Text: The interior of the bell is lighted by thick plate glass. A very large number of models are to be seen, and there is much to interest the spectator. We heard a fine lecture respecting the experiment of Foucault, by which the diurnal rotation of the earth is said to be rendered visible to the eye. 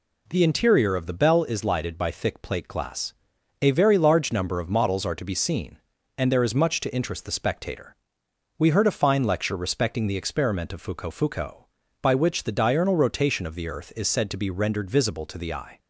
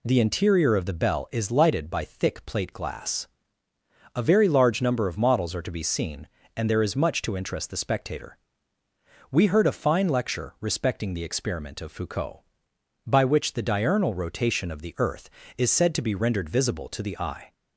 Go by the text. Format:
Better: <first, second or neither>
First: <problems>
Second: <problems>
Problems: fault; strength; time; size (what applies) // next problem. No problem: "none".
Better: second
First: says "Foucault" twice; at 11.1 s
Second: none